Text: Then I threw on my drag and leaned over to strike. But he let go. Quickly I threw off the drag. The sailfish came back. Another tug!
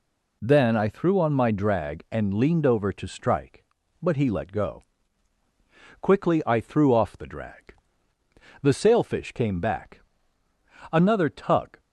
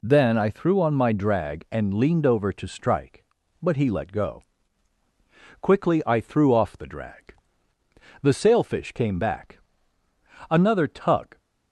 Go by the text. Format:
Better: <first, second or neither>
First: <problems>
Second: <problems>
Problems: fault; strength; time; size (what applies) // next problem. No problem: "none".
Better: neither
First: none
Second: none